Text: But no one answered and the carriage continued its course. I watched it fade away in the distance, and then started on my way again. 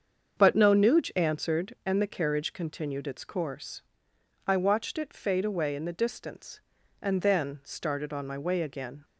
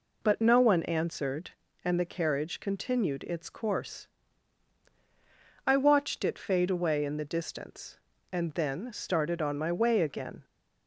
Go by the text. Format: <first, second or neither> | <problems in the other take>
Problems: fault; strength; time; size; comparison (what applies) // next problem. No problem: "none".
second | starts louder than the rest; strong; until 1.4 s; 7 dB // says "nuge" for "one"; at 0.7 s